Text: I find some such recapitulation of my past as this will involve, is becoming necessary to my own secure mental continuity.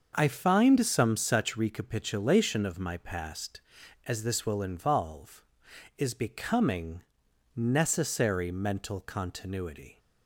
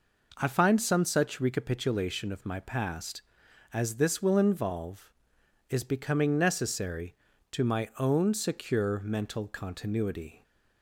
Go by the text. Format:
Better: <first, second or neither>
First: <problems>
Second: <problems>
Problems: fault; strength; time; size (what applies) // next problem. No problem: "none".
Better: second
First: starts louder than the rest; until 1.1 s; 6.5 dB // pauses between "becoming" and "necessary"; noticeable; at 7.0 s; 0.56 s long // skips "to my own secure"; at 8.5 s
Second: none